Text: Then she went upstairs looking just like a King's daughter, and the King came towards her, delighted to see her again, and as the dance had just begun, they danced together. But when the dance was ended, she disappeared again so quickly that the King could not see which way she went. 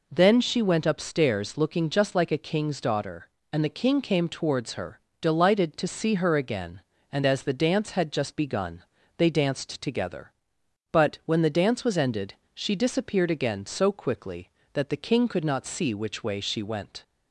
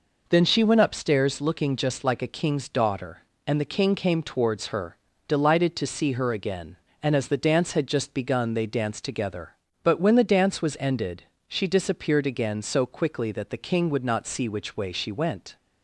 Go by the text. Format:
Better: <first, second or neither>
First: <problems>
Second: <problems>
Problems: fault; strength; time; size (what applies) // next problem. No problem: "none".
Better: first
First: none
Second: says "would" for "could"; at 13.9 s